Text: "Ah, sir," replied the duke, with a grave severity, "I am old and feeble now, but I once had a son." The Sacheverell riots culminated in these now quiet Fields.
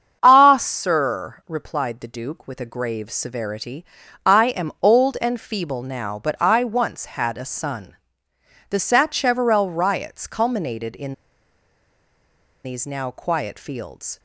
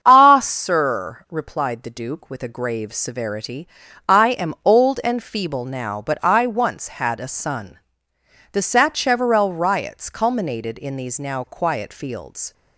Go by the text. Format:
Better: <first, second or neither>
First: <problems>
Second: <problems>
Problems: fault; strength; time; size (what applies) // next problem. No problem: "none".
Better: second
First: starts louder than the rest; strong; until 1.2 s; 7.5 dB // pauses between "in" and "these"; strong; at 11.1 s; 1.5 s long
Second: starts louder than the rest; strong; until 1.0 s; 7.5 dB